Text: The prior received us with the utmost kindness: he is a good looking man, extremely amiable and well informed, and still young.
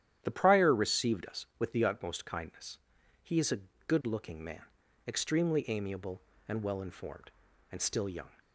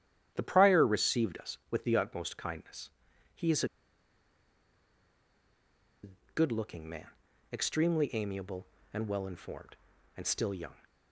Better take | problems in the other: first | starts louder than the rest; strong; until 1.3 s; 10.5 dB; strong in the first // pauses between "is" and "a"; strong; at 3.6 s; 2.3 s long // pauses between "a" and "good"; slight; at 6.0 s; 0.26 s long; slight in the first

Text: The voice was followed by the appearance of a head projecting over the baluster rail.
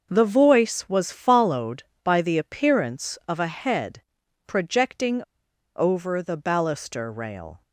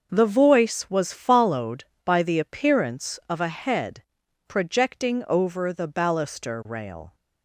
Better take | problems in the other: second | starts louder than the rest; until 1.1 s; 6 dB; noticeable in the second // pauses between "head" and "projecting"; noticeable; at 4.0 s; 0.46 s long; noticeable in the second // pauses between "projecting" and "over"; noticeable; at 5.2 s; 0.56 s long

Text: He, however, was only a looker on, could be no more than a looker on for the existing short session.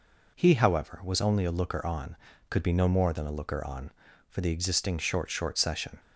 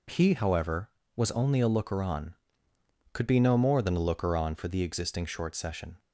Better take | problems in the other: second | says "short" twice; at 5.2 s

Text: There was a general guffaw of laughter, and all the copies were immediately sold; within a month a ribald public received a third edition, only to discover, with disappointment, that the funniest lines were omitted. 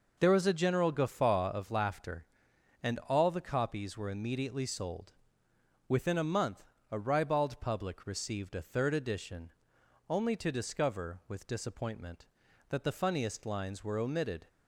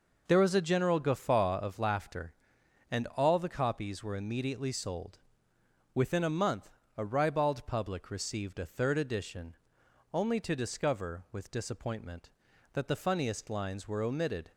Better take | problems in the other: neither | pauses between "month" and "a"; slight; the same in both

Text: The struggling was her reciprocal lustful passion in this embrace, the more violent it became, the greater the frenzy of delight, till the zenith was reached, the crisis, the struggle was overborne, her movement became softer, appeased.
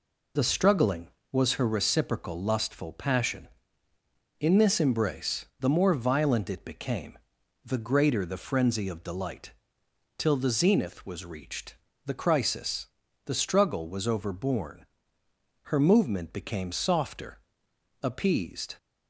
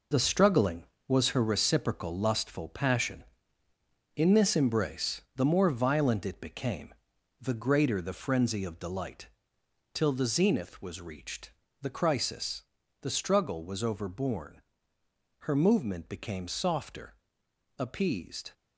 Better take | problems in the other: first | gets quieter; strong; throughout; 8.5 dB

